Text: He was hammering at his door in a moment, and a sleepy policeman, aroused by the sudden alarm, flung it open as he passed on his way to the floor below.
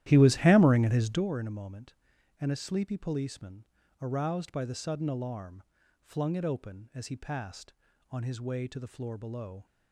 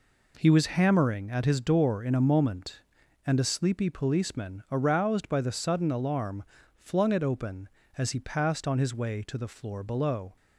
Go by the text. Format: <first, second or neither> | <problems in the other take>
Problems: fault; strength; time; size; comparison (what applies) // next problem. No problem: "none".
second | starts louder than the rest; strong; until 1.3 s; 13 dB